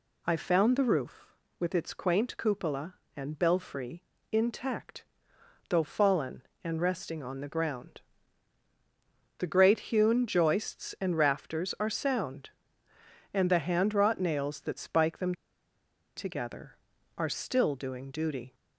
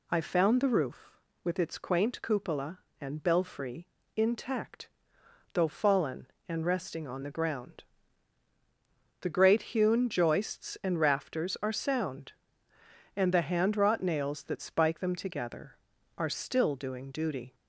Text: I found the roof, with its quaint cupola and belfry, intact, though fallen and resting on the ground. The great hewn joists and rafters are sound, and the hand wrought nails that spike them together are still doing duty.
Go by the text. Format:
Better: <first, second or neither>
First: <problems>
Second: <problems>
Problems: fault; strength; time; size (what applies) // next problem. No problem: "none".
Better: second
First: pauses between "them" and "together"; noticeable; at 15.3 s; 0.83 s long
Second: none